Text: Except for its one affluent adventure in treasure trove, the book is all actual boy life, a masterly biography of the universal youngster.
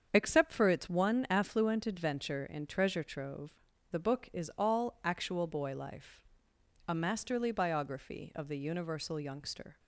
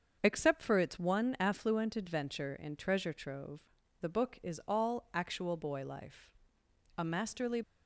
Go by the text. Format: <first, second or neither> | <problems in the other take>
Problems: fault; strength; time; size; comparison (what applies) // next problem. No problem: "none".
first | starts louder than the rest; until 1.2 s; 6.5 dB; strong in the first // stops before "biography of the universal youngster"; at 7.6 s